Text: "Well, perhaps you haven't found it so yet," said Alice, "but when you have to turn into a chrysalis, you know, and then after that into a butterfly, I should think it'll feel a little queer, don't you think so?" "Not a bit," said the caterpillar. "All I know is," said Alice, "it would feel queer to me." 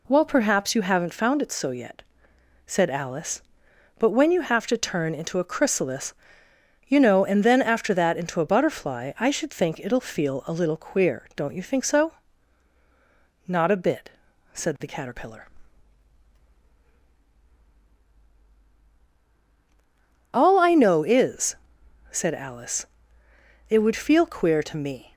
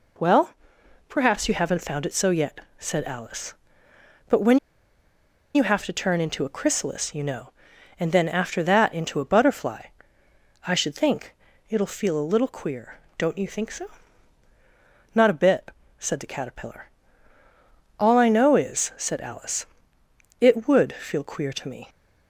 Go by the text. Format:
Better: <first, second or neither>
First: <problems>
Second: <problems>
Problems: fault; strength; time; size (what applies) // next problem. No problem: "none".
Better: first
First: none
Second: pauses between "when" and "you"; noticeable; at 4.5 s; 0.97 s long // pauses between "think" and "it'll"; slight; at 11.3 s; 0.34 s long